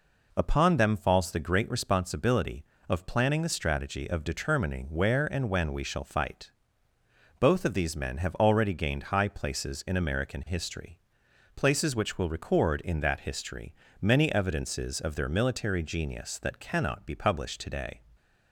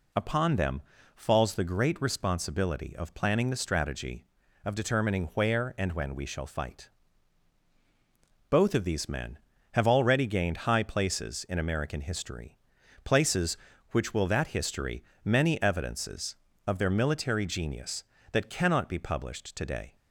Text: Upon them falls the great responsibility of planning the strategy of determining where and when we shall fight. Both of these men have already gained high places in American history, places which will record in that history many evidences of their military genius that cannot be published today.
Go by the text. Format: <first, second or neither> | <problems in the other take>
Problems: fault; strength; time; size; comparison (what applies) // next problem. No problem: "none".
first | pauses between "them" and "falls"; slight; at 0.8 s; 0.32 s long // skips "record in"; at 14.2 s // pauses between "history" and "many"; slight; at 15.0 s; 0.22 s long; slight in the first